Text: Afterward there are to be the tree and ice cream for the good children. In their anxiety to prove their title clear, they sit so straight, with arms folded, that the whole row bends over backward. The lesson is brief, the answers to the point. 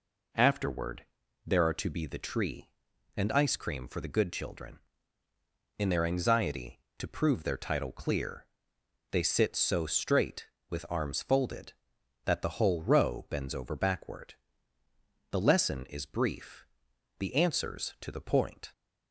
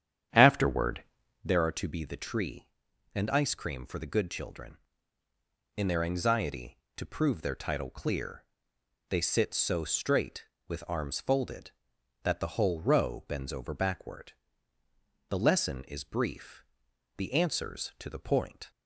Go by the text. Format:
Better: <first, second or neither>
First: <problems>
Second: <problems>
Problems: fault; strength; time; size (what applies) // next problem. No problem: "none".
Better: first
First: pauses between "Afterward" and "there"; at 1.0 s; 0.42 s long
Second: starts louder than the rest; strong; until 1.6 s; 9.5 dB // pauses between "Afterward" and "there"; at 1.0 s; 0.42 s long